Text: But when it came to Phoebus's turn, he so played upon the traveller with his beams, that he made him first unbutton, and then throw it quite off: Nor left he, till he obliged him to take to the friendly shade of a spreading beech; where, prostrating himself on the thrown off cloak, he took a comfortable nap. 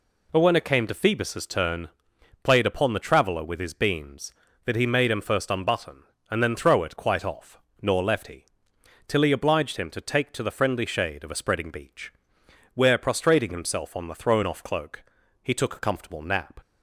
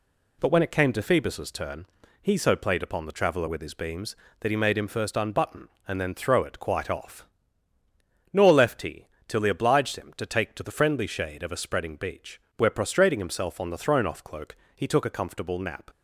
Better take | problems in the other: second | skips "he so"; at 2.1 s

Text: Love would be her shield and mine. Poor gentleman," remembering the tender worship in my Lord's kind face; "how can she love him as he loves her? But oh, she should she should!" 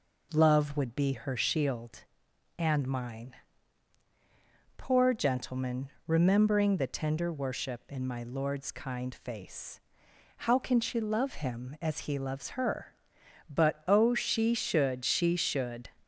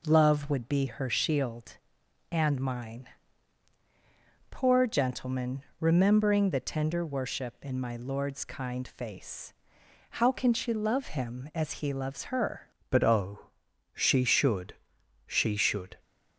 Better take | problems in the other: first | changes voice at "But"; from 12.8 s on; 3.1 s long // pauses between "should" and "she"; noticeable; at 14.7 s; 0.54 s long

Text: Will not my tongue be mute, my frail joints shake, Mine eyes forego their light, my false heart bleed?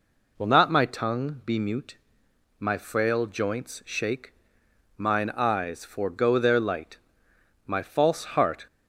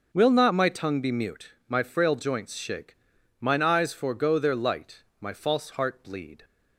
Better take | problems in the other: second | stops before "bleed"; at 8.6 s

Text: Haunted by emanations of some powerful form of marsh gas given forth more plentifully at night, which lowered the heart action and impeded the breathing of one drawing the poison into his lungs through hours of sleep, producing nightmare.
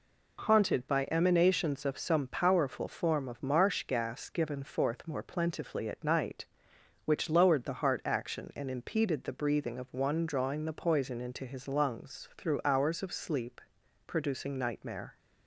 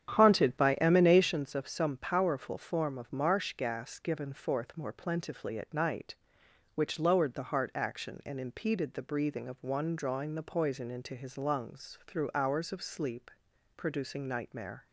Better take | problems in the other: first | starts louder than the rest; strong; until 1.4 s; 9.5 dB

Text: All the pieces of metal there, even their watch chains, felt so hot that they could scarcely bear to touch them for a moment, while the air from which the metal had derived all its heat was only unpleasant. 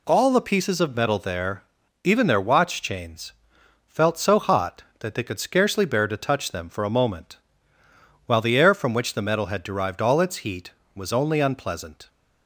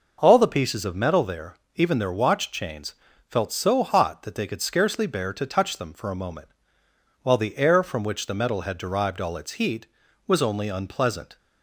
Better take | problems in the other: neither | none

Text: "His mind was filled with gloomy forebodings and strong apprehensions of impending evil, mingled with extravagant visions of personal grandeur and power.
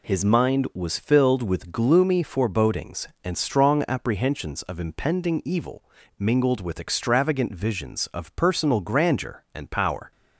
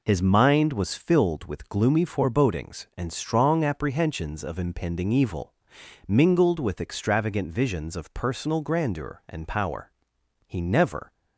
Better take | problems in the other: first | goes on to say "He never"; noticeable; from 10.4 s on; 0.66 s long

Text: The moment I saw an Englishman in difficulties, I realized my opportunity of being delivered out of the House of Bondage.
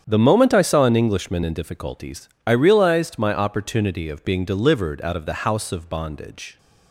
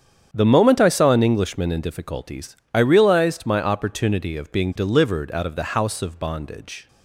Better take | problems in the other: neither | starts louder than the rest; strong; the same in both

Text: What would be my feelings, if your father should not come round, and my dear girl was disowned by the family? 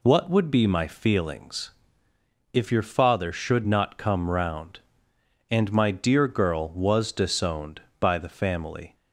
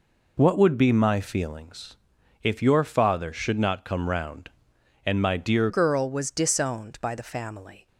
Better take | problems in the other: first | changes voice at "girl"; from 5.6 s on; 2.2 s long

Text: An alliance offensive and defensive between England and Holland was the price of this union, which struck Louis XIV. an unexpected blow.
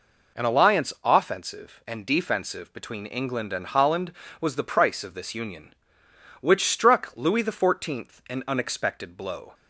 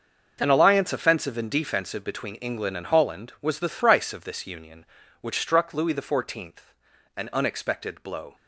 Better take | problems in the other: first | starts louder than the rest; noticeable; until 1.4 s; 6 dB // says "thrice" for "price"; at 3.6 s

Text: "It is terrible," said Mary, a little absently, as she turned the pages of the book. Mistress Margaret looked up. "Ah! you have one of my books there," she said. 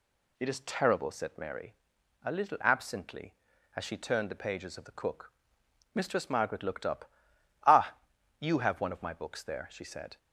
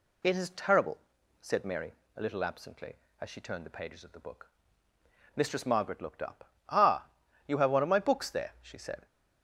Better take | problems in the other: second | says "cook" for "book"; at 4.9 s

